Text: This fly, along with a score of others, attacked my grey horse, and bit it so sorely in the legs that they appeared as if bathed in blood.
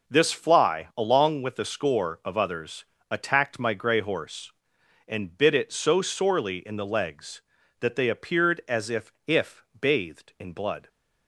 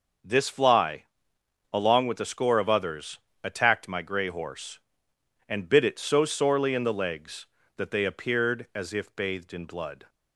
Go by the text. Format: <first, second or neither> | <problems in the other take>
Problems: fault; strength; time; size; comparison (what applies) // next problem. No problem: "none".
second | says "if" twice; at 9.2 s